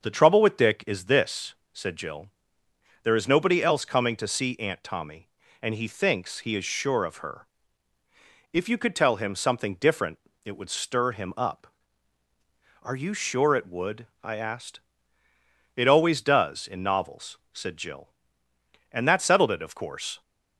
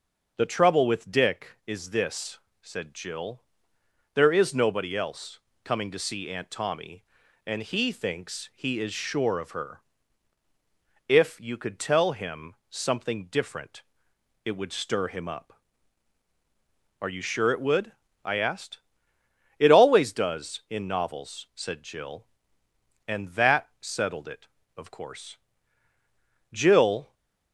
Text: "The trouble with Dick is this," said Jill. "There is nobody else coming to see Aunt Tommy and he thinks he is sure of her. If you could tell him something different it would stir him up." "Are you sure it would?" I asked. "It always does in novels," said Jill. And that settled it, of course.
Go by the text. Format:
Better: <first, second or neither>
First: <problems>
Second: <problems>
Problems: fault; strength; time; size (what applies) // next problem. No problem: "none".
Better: first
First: starts louder than the rest; until 1.0 s; 6.5 dB // pauses between "different" and "it"; slight; at 10.1 s; 0.28 s long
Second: starts louder than the rest; noticeable; until 1.3 s; 6 dB // pauses between "else" and "coming"; slight; at 5.3 s; 0.24 s long // pauses between "him" and "something"; slight; at 12.5 s; 0.16 s long // pauses between "different" and "it"; noticeable; at 13.8 s; 0.60 s long // goes on to say "Jill"; noticeable; from 26.5 s on; 0.62 s long